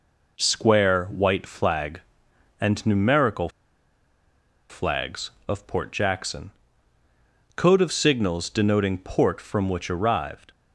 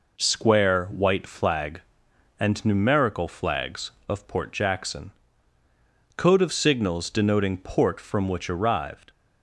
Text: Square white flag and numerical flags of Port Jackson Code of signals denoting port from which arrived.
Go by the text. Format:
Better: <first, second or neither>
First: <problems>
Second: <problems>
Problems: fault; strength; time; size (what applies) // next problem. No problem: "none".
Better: second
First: pauses between "numerical" and "flags"; at 3.4 s; 1.2 s long // pauses between "Jackson" and "Code"; at 6.5 s; 1.0 s long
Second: pauses between "Jackson" and "Code"; at 5.1 s; 1.0 s long